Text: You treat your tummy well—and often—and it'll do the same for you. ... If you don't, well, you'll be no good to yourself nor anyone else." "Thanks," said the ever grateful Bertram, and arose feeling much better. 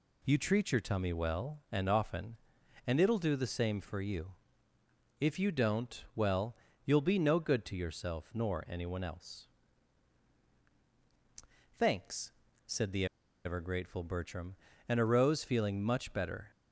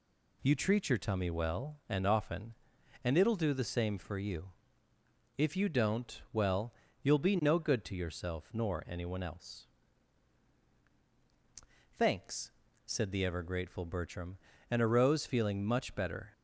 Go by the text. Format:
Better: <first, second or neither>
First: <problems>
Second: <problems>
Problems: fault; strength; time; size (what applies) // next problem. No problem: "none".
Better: second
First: pauses between "the" and "ever"; at 13.0 s; 0.39 s long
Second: none